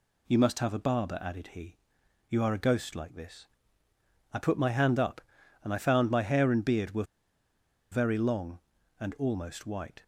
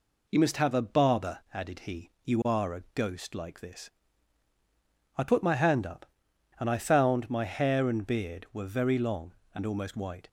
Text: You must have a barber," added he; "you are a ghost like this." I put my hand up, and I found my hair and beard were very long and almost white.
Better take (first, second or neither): second